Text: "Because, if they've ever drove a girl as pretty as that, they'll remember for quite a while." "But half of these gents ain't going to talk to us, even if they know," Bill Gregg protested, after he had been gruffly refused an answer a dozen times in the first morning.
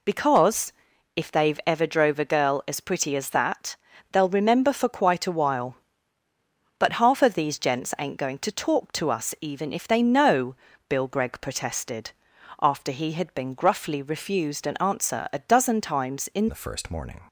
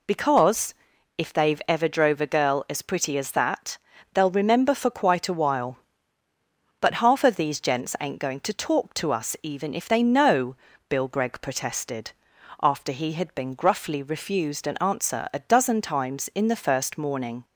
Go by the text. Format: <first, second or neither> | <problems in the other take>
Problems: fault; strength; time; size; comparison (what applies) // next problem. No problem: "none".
second | changes voice at "the"; from 16.4 s on; 0.8 s long